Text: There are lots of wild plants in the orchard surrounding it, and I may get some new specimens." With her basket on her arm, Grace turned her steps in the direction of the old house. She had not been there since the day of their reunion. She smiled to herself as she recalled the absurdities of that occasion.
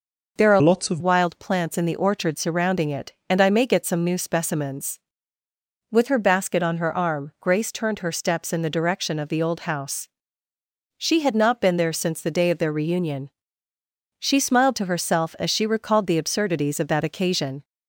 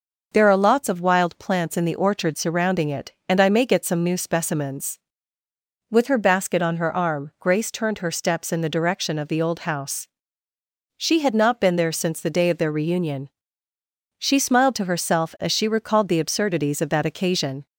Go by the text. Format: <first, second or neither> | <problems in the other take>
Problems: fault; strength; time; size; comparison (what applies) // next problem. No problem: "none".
second | changes voice from "lots" to "of"; from 0.6 to 0.9 s; 0.3 s long